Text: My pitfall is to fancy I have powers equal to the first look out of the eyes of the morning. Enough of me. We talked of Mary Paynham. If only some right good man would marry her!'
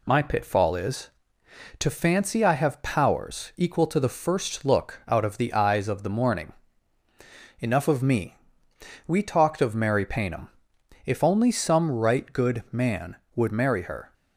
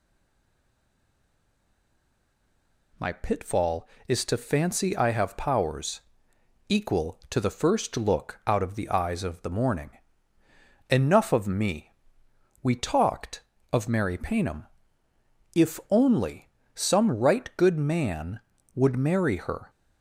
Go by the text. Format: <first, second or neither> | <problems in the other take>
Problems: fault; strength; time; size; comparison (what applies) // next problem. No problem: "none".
first | stays silent before the first word; strong; until 2.9 s; 2.9 s long // pauses between "powers" and "equal"; noticeable; at 5.9 s; 0.68 s long // pauses between "only" and "some"; slight; at 16.4 s; 0.26 s long